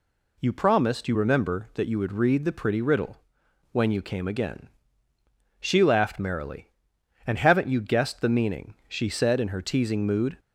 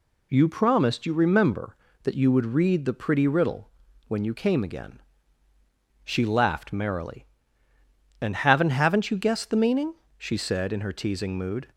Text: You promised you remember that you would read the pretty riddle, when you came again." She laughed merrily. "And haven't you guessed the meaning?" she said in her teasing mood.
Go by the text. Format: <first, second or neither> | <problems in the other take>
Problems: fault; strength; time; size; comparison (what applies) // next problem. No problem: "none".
first | says "haven't" twice; at 8.6 s